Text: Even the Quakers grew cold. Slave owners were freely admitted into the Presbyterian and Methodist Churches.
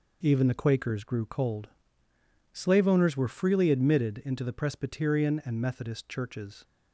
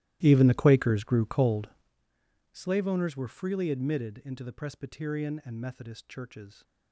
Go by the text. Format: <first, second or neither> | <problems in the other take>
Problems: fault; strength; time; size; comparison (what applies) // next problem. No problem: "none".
first | starts louder than the rest; strong; until 2.0 s; 15 dB